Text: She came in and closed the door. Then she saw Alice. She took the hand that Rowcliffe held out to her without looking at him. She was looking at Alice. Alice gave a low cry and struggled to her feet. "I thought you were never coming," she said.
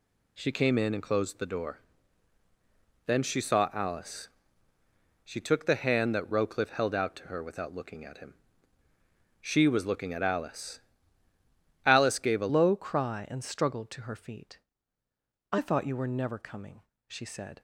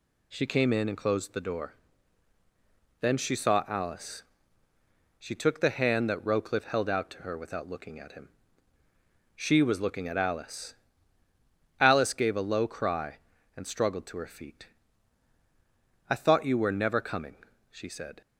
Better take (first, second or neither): second